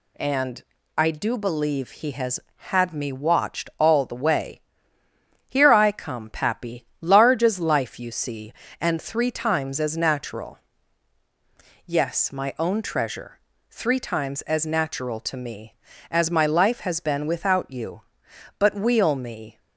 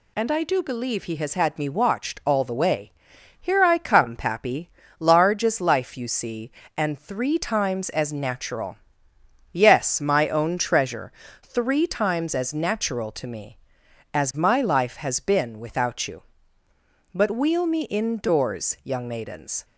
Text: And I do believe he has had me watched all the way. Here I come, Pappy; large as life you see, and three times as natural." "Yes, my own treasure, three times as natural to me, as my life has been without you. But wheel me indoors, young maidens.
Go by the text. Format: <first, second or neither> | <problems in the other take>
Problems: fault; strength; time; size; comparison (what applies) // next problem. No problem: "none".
second | pauses between "And" and "I"; slight; at 0.6 s; 0.36 s long // stops before "indoors young maidens"; at 19.5 s